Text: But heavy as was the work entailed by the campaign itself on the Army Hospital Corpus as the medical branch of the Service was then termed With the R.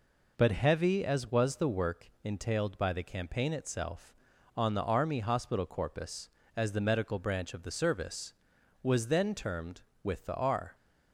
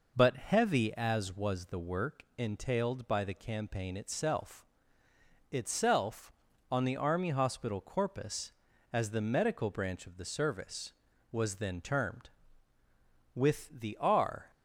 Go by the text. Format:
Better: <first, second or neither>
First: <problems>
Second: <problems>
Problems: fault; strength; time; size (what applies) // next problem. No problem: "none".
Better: first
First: none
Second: says "itself" twice; at 5.5 s